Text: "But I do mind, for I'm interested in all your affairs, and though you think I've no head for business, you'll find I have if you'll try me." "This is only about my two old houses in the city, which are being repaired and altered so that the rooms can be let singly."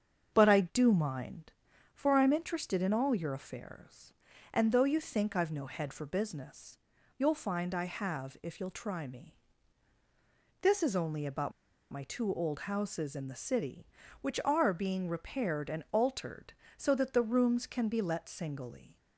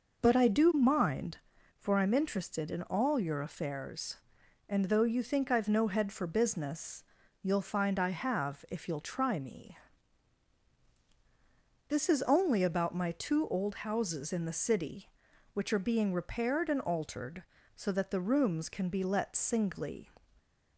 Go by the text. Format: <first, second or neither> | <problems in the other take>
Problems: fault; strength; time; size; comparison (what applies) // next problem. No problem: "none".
second | starts louder than the rest; strong; until 1.3 s; 7 dB // pauses between "about" and "my"; at 11.5 s; 0.40 s long